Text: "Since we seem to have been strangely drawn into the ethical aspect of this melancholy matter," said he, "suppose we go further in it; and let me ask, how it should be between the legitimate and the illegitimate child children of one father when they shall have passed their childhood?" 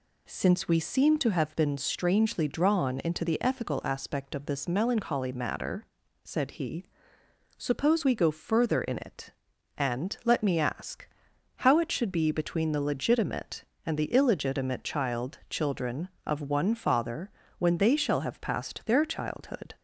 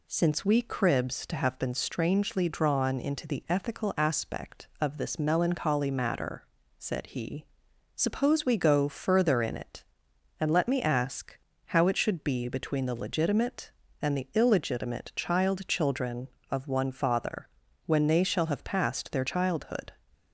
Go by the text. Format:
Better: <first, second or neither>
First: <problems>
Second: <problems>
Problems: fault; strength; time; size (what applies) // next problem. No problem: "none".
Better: first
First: pauses between "father" and "when"; slight; at 17.2 s; 0.28 s long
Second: says "cribs" for "seem"; at 0.6 s // pauses between "father" and "when"; at 17.4 s; 0.40 s long